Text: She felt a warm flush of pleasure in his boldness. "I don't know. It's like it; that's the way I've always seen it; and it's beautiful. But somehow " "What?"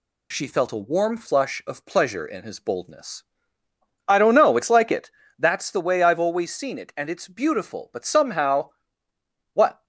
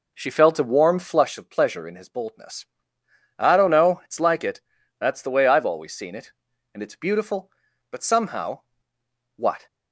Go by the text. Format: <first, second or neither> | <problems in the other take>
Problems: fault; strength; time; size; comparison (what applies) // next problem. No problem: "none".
first | starts louder than the rest; noticeable; until 1.4 s; 4.5 dB